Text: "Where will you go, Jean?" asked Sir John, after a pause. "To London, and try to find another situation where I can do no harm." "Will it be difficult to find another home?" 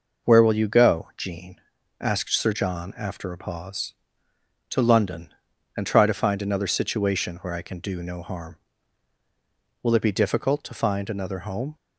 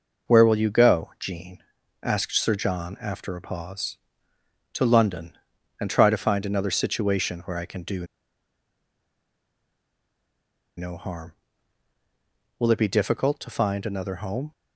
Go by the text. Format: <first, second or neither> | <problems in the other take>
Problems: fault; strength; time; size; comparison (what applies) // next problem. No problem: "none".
first | pauses between "do" and "no"; strong; at 8.0 s; 2.7 s long